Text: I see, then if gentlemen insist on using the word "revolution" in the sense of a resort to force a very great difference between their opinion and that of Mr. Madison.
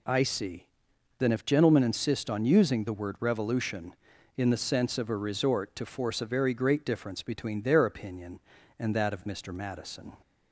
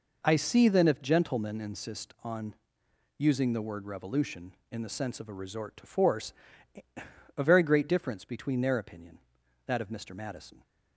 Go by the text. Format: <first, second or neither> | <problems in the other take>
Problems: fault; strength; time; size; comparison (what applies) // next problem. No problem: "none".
first | pauses between "on" and "using"; noticeable; at 2.5 s; 0.64 s long // pauses between "force" and "a"; at 6.3 s; 1.0 s long // skips "and"; at 9.4 s